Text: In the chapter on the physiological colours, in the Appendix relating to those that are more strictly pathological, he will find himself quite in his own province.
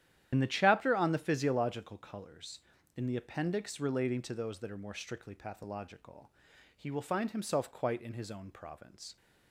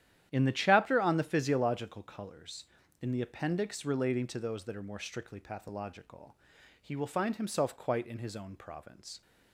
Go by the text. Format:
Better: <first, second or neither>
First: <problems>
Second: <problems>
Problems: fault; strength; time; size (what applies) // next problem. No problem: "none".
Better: second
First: loses the start of "In"; at 0.3 s; 65 ms // starts louder than the rest; strong; until 1.3 s; 11 dB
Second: starts louder than the rest; strong; until 1.3 s; 11 dB